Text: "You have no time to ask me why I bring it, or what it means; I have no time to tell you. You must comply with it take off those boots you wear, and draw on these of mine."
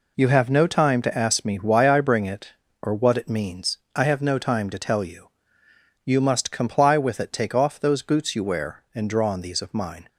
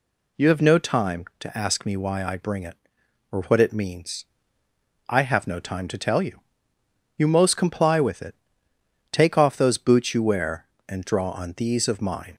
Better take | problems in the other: first | says "most" for "must"; at 7.2 s // pauses between "it" and "take"; noticeable; at 8.3 s; 0.76 s long

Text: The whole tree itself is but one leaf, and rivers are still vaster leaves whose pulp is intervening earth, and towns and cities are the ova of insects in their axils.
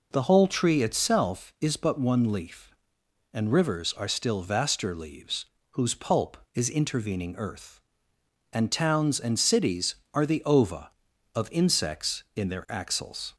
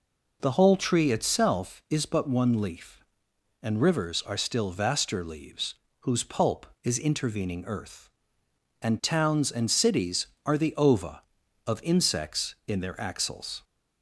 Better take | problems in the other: neither | pauses between "leaves" and "whose"; slight; the same in both

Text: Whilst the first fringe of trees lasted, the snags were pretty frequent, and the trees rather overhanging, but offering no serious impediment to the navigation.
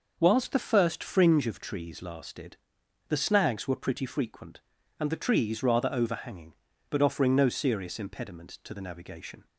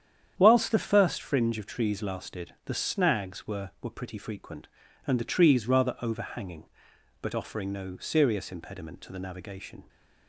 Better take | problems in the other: first | starts louder than the rest; strong; until 1.3 s; 9 dB // says "were" twice; at 3.8 s

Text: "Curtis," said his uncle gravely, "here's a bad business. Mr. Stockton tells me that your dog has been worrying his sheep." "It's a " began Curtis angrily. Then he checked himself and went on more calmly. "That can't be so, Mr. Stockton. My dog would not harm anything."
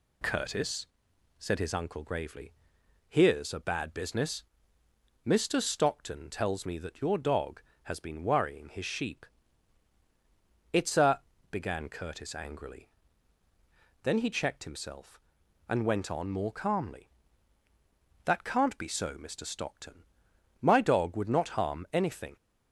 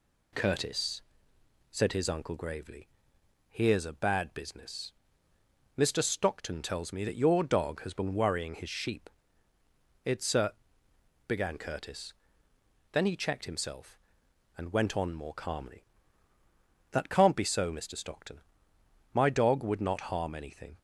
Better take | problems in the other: first | skips "angrily"; at 12.5 s

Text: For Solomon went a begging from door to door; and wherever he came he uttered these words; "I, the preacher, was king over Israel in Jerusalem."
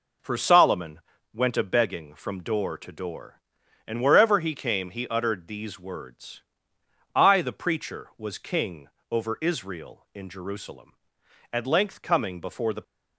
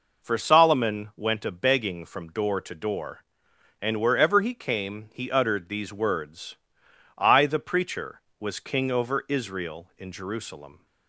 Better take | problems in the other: second | pauses between "Solomon" and "went"; slight; at 1.0 s; 0.32 s long // pauses between "king" and "over"; slight; at 8.8 s; 0.22 s long // goes on to say "At length coming before the"; from 11.5 s on; 1.3 s long

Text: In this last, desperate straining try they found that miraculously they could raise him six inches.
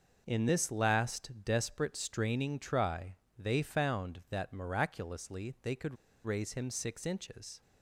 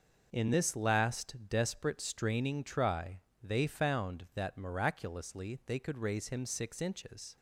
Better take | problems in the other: second | pauses between "try" and "they"; slight; at 3.1 s; 0.24 s long; slight in the second // pauses between "could" and "raise"; slight; at 5.9 s; 0.29 s long

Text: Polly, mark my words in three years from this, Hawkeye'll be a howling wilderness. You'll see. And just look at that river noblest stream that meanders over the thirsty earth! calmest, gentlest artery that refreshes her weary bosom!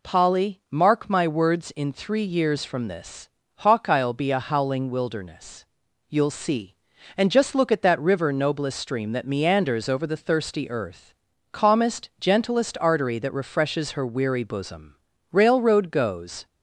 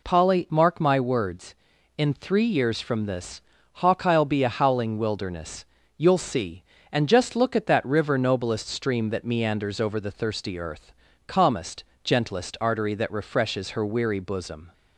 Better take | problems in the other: second | goes on to say "Railroad goes"; noticeable; from 15.3 s on; 1.1 s long

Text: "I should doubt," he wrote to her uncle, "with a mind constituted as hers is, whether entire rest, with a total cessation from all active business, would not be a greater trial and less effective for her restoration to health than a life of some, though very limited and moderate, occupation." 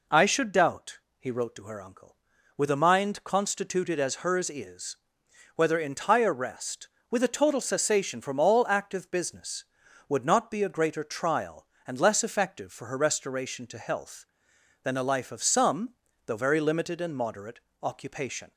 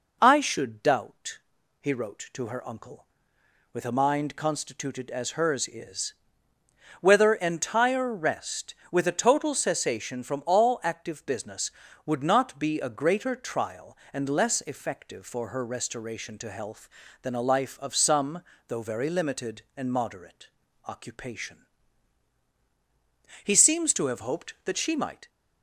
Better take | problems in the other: first | goes on to say "He seems to have hoped that she might"; strong; from 23.4 s on; 1.8 s long

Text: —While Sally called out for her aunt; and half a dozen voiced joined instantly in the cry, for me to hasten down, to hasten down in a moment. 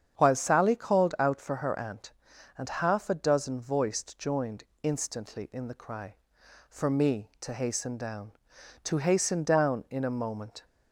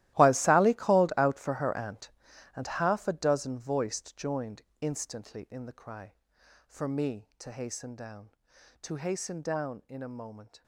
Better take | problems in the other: first | gets quieter; strong; throughout; 16 dB // starts louder than the rest; strong; until 1.1 s; 15 dB; strong in the first // pauses between "joined" and "instantly"; slight; at 4.6 s; 0.20 s long; slight in the first

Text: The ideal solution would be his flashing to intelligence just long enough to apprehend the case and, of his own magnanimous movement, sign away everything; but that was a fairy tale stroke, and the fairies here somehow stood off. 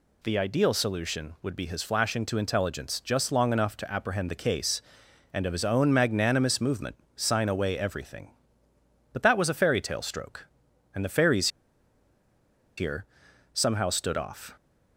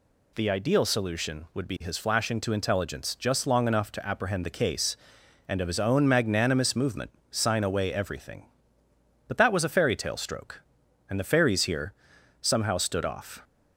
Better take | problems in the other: second | pauses between "fairies" and "here"; strong; at 11.4 s; 1.2 s long // pauses between "here" and "somehow"; noticeable; at 13.0 s; 0.48 s long; noticeable in the second

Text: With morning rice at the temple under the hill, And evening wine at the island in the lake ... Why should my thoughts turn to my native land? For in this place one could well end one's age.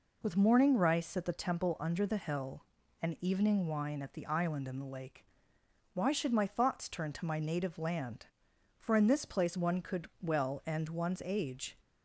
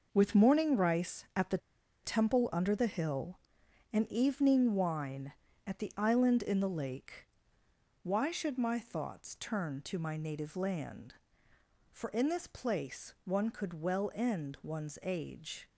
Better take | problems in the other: first | pauses between "the" and "temple"; at 1.5 s; 0.45 s long

